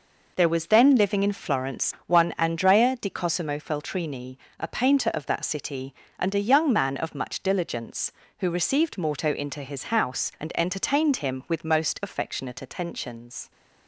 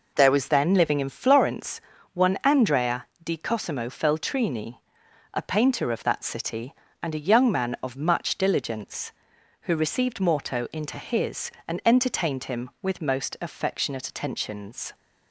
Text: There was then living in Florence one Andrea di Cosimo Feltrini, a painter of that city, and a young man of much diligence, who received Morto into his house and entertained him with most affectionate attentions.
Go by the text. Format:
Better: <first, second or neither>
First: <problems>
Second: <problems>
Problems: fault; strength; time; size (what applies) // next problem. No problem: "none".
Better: first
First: none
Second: pauses between "Florence" and "one"; slight; at 1.8 s; 0.32 s long // pauses between "Andrea" and "di"; slight; at 3.0 s; 0.16 s long // skips "house"; at 11.5 s